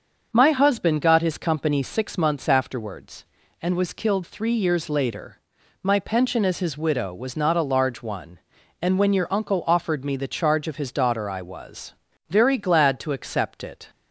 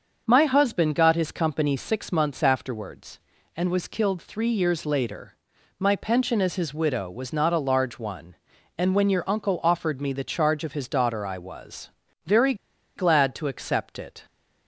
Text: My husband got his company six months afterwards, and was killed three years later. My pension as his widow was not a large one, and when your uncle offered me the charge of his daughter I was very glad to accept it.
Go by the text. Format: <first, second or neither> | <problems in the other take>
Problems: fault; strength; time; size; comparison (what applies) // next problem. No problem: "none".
first | starts louder than the rest; until 1.2 s; 6.5 dB; also in the first // pauses between "was" and "very"; slight; at 11.9 s; 0.34 s long; slight in the first // pauses between "very" and "glad"; at 12.5 s; 0.41 s long